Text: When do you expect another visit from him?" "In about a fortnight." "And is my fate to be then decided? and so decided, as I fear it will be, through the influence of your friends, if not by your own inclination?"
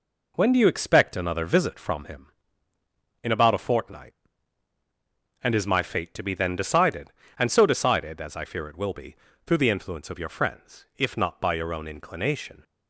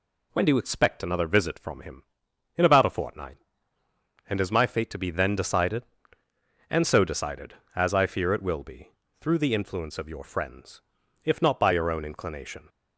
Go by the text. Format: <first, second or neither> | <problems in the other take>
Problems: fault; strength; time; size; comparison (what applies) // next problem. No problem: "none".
second | gets quieter; noticeable; throughout; 4.5 dB